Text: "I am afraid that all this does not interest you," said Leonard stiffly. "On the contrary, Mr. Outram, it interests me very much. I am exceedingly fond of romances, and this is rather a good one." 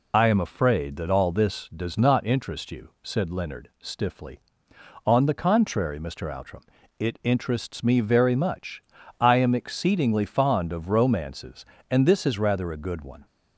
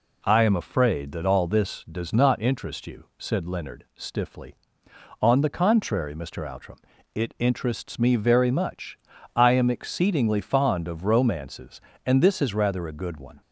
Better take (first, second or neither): second